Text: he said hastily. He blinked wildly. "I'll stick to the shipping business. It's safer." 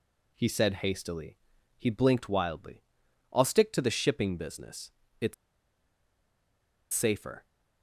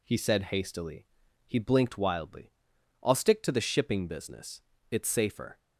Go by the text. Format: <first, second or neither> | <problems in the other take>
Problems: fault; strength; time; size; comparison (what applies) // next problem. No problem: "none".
second | pauses between "It's" and "safer"; strong; at 5.3 s; 1.5 s long